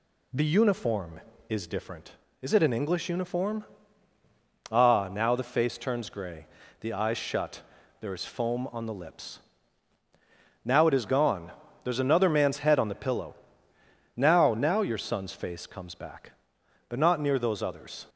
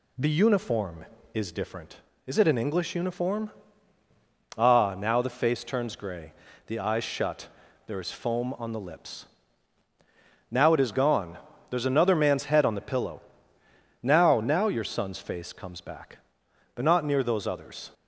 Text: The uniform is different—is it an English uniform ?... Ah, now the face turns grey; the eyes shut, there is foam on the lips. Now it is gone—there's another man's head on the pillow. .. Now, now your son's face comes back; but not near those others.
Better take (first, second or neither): neither